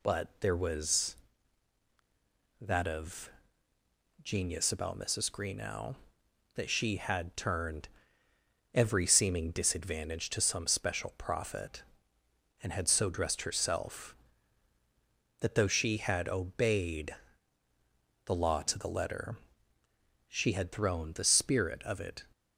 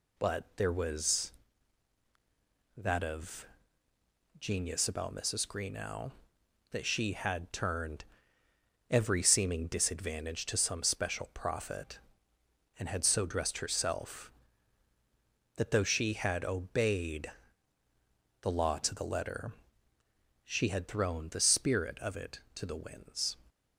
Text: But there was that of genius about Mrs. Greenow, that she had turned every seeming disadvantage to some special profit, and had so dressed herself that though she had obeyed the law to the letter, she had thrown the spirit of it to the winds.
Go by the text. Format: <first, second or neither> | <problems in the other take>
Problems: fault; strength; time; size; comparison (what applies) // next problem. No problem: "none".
second | pauses between "of" and "genius"; noticeable; at 3.3 s; 0.92 s long; noticeable in the second // pauses between "turned" and "every"; noticeable; at 7.8 s; 0.86 s long; noticeable in the second // pauses between "obeyed" and "the"; at 17.1 s; 1.1 s long; also in the second // stops before "to the winds"; at 22.3 s